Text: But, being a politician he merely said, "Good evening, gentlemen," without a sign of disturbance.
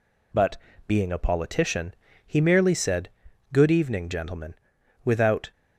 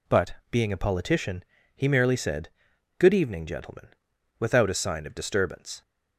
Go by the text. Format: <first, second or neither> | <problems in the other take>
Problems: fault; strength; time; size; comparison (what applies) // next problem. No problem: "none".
second | pauses between "politician" and "he"; slight; at 1.9 s; 0.32 s long; slight in the second // stops before "a sign of disturbance"; at 5.5 s